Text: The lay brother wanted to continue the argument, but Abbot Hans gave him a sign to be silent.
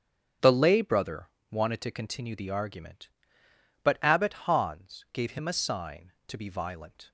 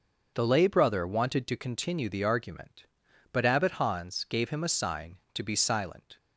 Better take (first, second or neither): second